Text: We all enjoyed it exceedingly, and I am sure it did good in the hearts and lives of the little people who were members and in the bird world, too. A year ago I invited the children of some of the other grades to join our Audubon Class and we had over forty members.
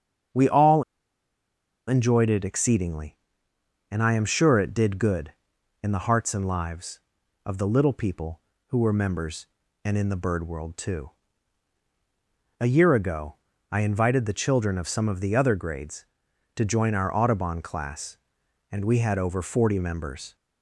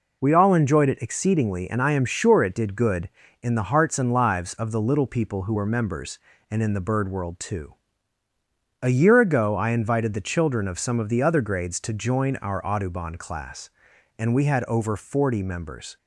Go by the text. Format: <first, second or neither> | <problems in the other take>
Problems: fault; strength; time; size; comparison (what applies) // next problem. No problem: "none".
second | starts louder than the rest; strong; until 2.3 s; 8 dB // pauses between "all" and "enjoyed"; at 0.8 s; 1.0 s long // pauses between "ago" and "I"; slight; at 13.3 s; 0.34 s long